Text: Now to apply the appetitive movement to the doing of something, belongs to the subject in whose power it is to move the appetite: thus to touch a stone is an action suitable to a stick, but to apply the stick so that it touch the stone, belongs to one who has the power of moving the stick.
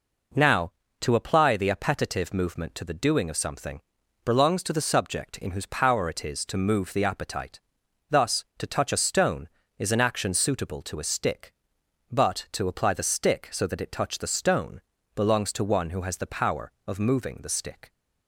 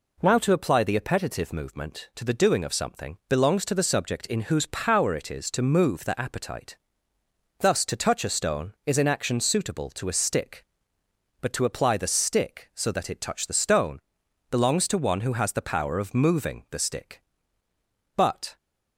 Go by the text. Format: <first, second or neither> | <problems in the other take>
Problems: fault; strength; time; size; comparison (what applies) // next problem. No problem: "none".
first | goes on to say "But"; slight; from 18.1 s on; 0.40 s long